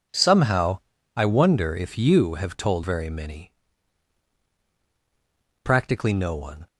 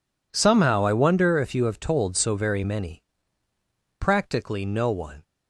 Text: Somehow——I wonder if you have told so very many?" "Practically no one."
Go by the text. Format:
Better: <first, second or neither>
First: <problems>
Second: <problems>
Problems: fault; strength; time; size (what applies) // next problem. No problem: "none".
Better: second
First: skips "so"; at 2.8 s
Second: none